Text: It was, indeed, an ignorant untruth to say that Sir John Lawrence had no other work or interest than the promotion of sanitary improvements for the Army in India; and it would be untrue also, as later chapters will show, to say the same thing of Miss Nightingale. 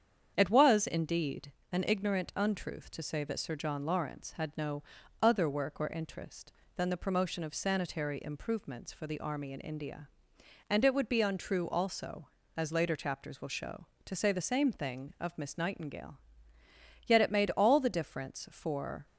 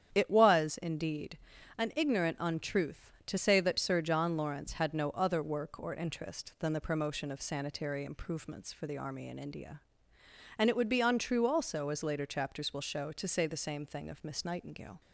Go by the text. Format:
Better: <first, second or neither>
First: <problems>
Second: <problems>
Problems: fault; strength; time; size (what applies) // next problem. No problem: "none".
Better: second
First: starts louder than the rest; strong; until 1.3 s; 8 dB // pauses between "no" and "other"; at 4.8 s; 0.38 s long // goes on to say "Yet it made all the difference for"; strong; from 17.0 s on; 2.0 s long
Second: starts louder than the rest; strong; until 1.1 s; 9 dB